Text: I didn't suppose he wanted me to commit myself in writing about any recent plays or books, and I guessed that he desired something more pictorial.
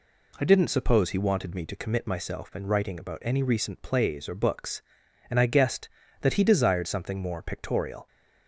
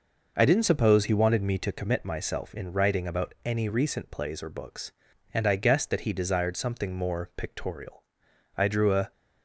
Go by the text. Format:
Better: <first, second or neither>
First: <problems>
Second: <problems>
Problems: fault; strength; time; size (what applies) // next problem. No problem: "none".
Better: first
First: none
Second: goes on to say "I drew a"; from 8.5 s on; 0.56 s long